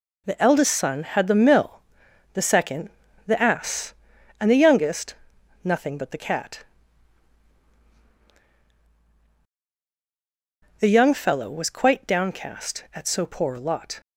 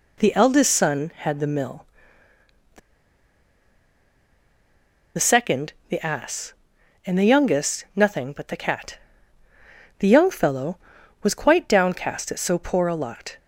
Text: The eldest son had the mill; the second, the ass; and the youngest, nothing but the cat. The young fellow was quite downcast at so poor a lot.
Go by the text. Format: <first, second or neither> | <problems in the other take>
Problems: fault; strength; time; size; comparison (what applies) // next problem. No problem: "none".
first | pauses between "the" and "second"; strong; at 2.7 s; 2.3 s long